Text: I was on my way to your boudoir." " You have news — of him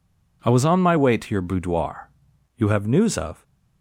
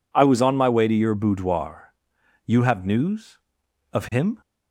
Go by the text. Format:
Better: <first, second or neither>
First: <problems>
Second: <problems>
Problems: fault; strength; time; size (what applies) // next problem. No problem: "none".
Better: second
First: stops before "him"; at 3.4 s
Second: none